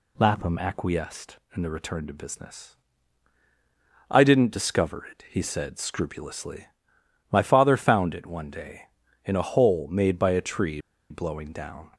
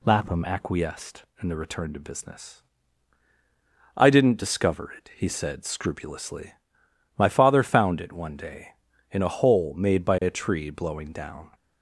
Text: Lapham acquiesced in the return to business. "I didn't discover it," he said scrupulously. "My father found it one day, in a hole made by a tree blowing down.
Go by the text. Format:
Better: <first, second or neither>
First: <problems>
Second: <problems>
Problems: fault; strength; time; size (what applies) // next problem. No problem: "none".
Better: second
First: pauses between "tree" and "blowing"; slight; at 10.7 s; 0.31 s long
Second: none